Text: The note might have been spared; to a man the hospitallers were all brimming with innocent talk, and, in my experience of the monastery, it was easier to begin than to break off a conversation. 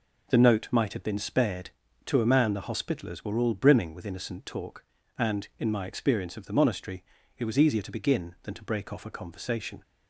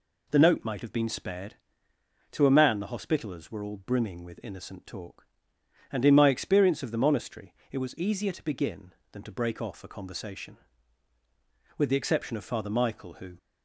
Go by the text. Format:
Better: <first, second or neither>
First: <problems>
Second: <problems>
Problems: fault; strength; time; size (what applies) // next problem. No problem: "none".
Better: first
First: none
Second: goes on to say "With the exception of Father Michael who"; from 11.7 s on; 1.6 s long